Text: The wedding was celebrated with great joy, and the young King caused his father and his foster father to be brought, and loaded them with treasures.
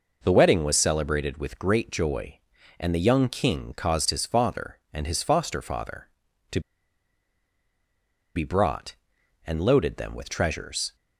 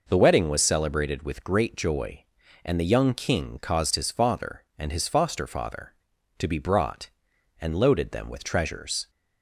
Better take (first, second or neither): second